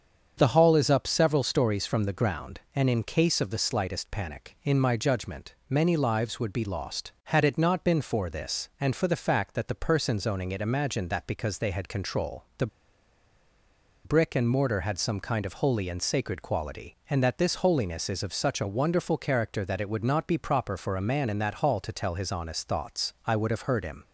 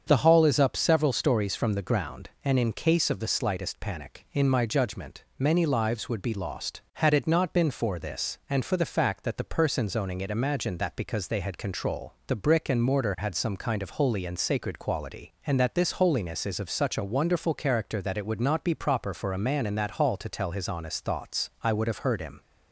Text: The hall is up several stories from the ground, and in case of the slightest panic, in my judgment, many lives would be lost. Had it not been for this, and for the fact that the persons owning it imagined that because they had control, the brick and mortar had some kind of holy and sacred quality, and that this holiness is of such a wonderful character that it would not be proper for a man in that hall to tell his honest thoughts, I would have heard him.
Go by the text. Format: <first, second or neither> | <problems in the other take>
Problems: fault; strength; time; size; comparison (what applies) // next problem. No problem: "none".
second | starts louder than the rest; strong; until 1.3 s; 7 dB; strong in the second // pauses between "the" and "brick"; strong; at 12.6 s; 1.3 s long